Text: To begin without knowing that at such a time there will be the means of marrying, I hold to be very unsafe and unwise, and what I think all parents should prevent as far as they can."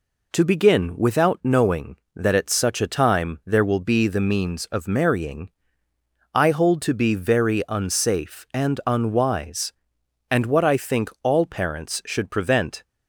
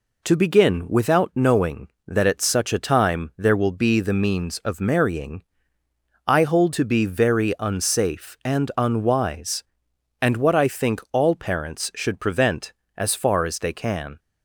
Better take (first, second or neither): second